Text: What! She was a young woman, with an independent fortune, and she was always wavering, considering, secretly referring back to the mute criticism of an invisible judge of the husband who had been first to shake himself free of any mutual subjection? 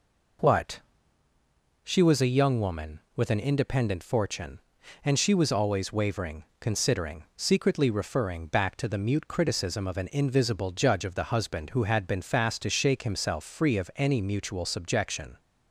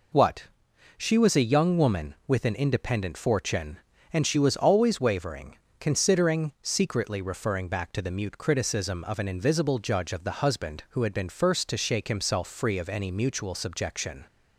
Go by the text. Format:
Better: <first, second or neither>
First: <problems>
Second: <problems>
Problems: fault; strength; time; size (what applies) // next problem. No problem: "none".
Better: second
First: says "fast" for "first"; at 12.2 s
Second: none